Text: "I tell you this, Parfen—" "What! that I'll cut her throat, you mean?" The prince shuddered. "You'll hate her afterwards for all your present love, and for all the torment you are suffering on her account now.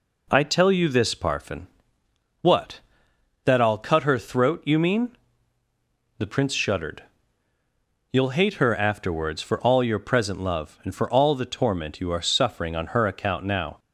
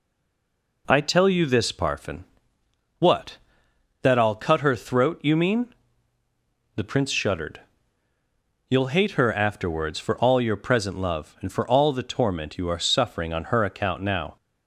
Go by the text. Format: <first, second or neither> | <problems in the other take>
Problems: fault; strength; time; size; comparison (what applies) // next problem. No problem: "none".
first | stays silent before the first word; slight; until 0.8 s; 0.8 s long